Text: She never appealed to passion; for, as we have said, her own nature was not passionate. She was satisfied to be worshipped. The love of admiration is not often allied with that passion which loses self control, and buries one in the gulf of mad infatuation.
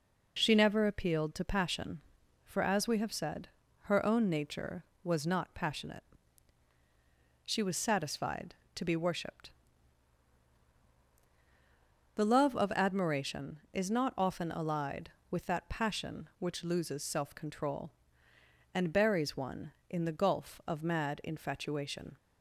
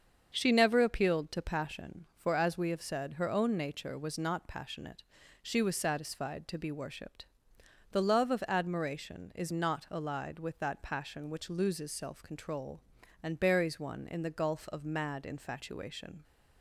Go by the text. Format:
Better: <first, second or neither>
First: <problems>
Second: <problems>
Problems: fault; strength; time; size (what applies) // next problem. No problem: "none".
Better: first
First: none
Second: starts louder than the rest; until 1.3 s; 7 dB // skips "often"; at 9.8 s